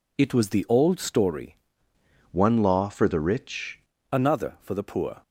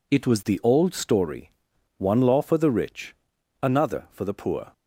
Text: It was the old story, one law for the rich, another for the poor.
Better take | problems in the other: second | changes voice from "one" to "rich"; from 2.3 to 3.7 s; 1.4 s long

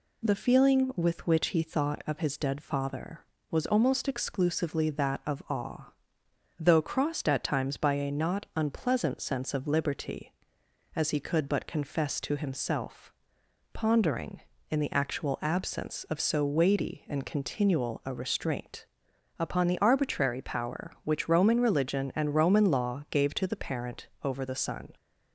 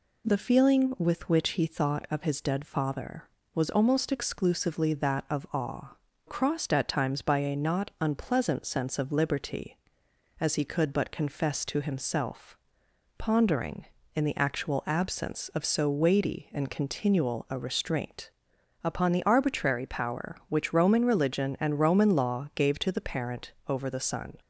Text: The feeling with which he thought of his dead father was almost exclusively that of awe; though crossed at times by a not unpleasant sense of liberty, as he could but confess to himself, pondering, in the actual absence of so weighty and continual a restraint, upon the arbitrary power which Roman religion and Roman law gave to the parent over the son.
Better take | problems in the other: first | skips "though"; at 6.1 s // pauses between "parent" and "over"; slight; at 23.5 s; 0.16 s long; slight in the first

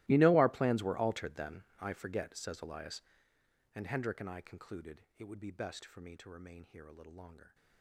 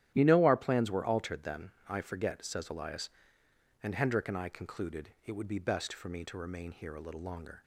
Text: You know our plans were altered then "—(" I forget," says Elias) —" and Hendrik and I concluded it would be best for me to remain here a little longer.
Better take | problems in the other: second | gets quieter; strong; throughout; 21 dB // starts louder than the rest; strong; until 1.1 s; 18 dB; strong in the second

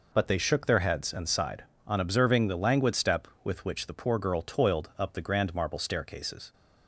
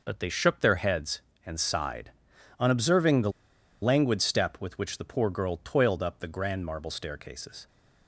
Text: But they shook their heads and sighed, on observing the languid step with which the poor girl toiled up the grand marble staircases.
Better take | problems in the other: first | pauses between "the" and "languid"; noticeable; at 3.3 s; 0.51 s long

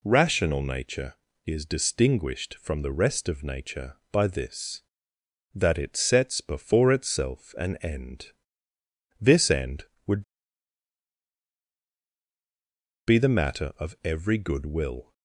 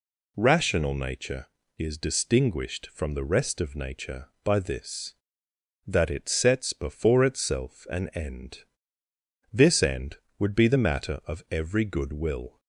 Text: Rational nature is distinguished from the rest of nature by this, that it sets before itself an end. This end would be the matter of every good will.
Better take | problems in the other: second | pauses between "would" and "be"; strong; at 10.2 s; 2.8 s long

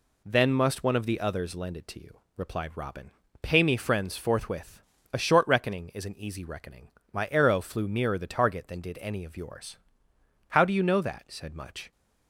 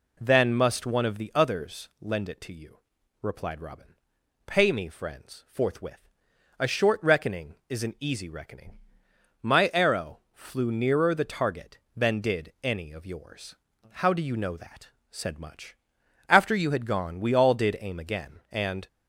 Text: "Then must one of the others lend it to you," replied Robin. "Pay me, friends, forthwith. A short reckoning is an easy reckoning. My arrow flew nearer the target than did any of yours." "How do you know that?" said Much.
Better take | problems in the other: first | goes on to say "After you had gone we all did aim again and"; strong; from 16.2 s on; 2.6 s long

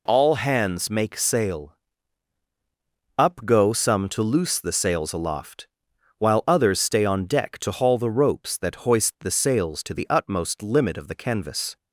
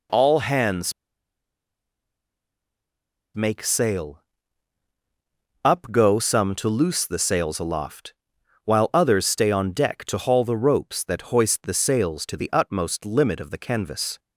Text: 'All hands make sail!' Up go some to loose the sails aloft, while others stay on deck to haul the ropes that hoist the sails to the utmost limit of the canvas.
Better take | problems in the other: first | pauses between "hands" and "make"; strong; at 0.9 s; 2.4 s long

